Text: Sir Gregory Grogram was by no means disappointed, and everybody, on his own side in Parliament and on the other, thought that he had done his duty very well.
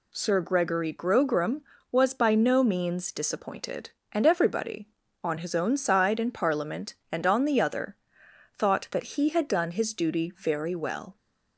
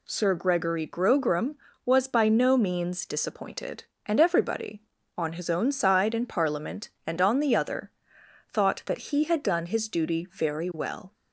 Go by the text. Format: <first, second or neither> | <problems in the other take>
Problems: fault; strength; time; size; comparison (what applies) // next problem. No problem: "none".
neither | none